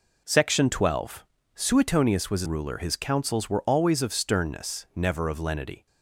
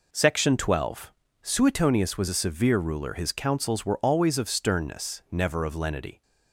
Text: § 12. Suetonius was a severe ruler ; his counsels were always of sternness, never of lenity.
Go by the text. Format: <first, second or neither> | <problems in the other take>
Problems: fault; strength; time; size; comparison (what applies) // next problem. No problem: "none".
second | skips "severe"; at 2.4 s